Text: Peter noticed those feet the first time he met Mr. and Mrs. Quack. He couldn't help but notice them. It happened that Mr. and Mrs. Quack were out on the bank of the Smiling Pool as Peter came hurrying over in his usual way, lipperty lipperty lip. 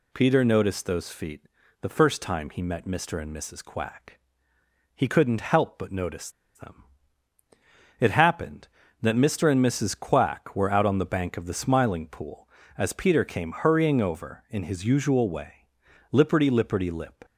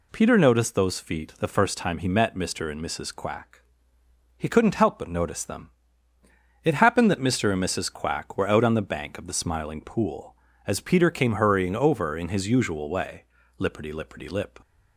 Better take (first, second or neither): second